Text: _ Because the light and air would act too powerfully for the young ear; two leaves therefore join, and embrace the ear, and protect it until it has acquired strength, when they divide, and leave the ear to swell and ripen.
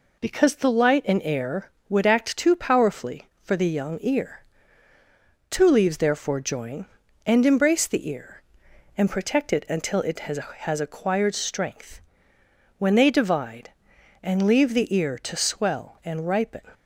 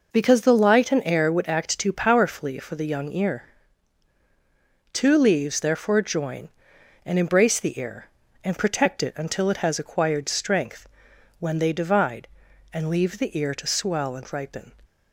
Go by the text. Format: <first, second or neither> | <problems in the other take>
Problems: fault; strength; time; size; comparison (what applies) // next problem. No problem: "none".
second | says "has" twice; at 10.4 s